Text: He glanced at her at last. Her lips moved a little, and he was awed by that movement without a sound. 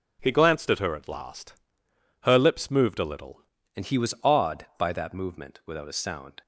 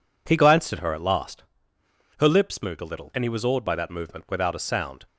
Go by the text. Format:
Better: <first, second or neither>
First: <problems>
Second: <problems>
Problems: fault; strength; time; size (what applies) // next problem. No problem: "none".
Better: second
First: changes voice at "and"; from 3.7 s on; 2.7 s long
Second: none